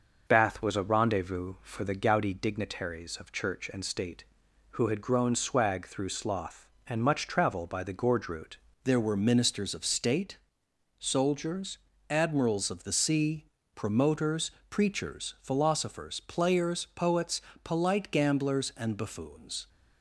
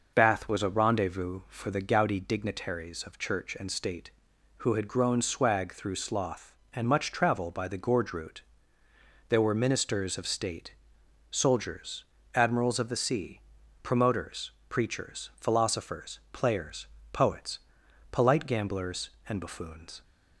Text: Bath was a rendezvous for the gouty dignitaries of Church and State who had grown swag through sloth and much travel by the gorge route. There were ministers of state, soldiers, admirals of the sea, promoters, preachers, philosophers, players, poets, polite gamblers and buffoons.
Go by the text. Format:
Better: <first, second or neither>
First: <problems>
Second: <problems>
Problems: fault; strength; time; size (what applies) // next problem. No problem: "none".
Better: second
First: starts louder than the rest; noticeable; until 1.2 s; 6 dB // changes voice at "There"; from 8.8 s on; 10.8 s long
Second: none